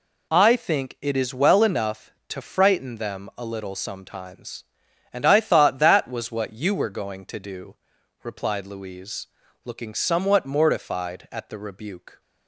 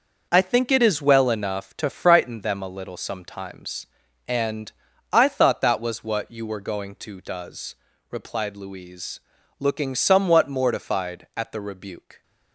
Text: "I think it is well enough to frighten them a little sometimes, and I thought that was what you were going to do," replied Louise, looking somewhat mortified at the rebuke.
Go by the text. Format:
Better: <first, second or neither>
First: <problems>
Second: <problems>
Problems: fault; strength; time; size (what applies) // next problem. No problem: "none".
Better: first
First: none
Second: starts louder than the rest; noticeable; until 1.3 s; 6 dB // pauses between "and" and "I"; at 4.7 s; 0.40 s long // says "does" for "do"; at 7.2 s